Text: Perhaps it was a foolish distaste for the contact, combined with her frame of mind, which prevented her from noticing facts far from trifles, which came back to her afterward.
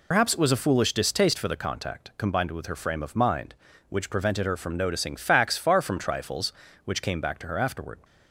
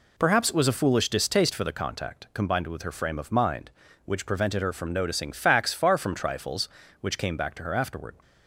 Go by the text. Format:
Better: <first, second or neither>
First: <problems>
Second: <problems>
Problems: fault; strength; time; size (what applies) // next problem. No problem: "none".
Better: second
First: loses the start of "Perhaps"; at 0.1 s; 90 ms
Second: none